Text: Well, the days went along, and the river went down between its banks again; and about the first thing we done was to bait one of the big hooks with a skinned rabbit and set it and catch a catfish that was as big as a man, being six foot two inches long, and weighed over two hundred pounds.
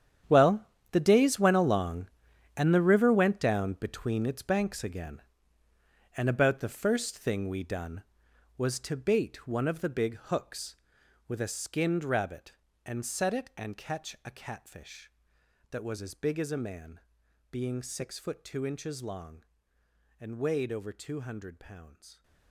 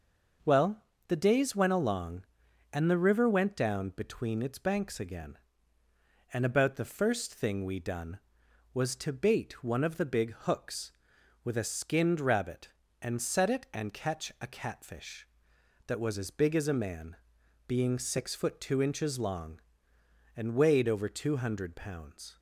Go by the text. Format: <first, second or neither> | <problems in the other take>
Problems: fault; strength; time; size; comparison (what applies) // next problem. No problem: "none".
second | gets quieter; strong; throughout; 15.5 dB